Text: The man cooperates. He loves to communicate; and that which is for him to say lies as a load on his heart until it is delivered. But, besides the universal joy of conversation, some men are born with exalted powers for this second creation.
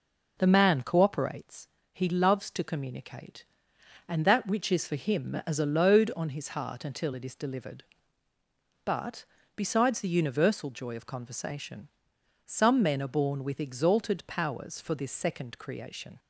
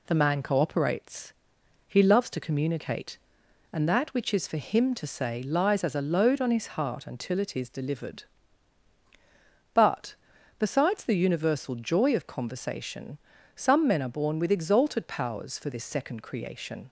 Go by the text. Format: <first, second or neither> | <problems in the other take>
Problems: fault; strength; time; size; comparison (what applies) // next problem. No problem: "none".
second | skips "to say lies"; at 5.4 s